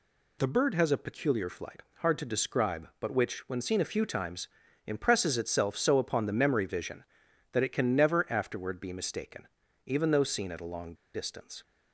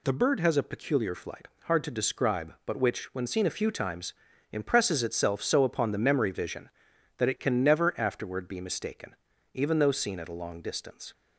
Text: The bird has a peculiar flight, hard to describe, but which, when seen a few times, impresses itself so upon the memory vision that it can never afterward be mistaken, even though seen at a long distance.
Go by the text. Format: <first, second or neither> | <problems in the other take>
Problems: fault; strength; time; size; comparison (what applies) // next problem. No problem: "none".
second | pauses between "long" and "distance"; slight; at 10.9 s; 0.20 s long